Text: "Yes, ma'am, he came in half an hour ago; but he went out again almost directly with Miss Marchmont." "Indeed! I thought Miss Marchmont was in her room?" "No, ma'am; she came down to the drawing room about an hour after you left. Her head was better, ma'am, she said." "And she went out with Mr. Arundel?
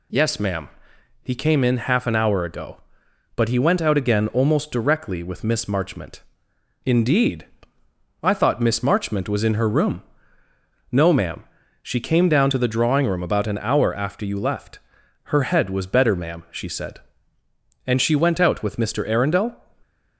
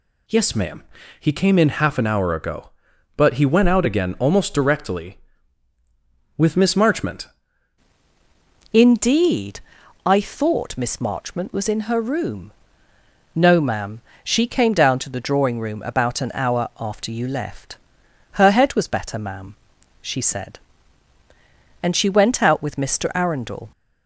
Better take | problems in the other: first | changes voice at "Indeed"; from 8.7 s on; 15.0 s long

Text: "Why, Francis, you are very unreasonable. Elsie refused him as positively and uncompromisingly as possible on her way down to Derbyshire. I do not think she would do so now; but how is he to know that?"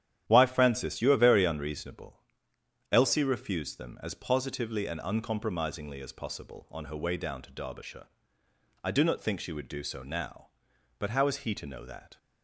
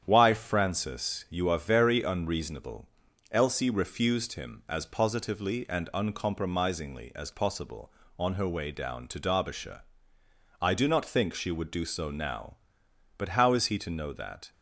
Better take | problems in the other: second | starts louder than the rest; strong; until 1.3 s; 11 dB; strong in the second // says "them" for "him"; at 3.7 s

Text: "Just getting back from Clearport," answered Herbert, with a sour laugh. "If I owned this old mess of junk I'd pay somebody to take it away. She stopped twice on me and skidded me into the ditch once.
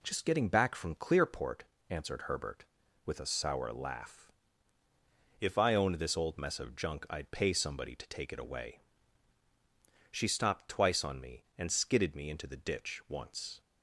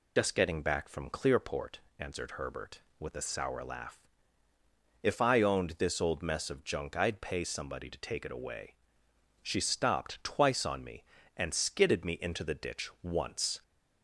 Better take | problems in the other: first | loses the start of "Just"; at 0.1 s; 50 ms

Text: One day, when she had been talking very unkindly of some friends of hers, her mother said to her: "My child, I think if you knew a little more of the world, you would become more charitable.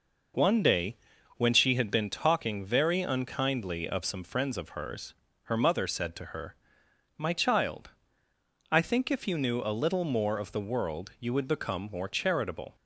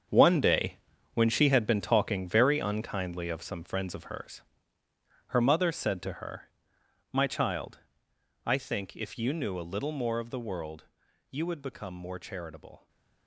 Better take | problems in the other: first | gets quieter; strong; throughout; 11.5 dB

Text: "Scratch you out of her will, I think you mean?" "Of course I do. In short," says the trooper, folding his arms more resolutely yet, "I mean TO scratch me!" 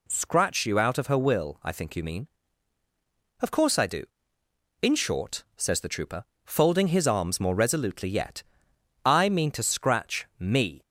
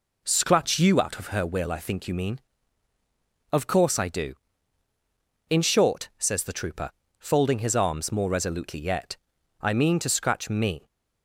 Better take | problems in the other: neither | none

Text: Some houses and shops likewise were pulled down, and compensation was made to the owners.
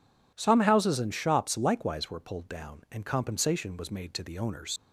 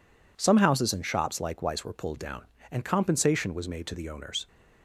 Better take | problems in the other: second | leaves "owners" unfinished; at 4.7 s; 45 ms

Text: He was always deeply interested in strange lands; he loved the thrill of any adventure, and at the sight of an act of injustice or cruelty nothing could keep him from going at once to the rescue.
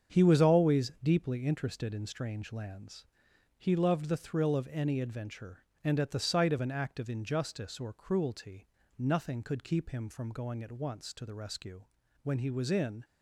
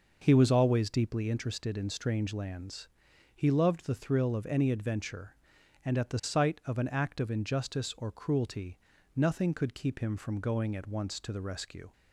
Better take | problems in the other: second | starts louder than the rest; strong; until 1.2 s; 7.5 dB // pauses between "cruelty" and "nothing"; slight; at 8.6 s; 0.32 s long; also in the second // goes on to say "When he was in"; noticeable; from 12.2 s on; 0.80 s long

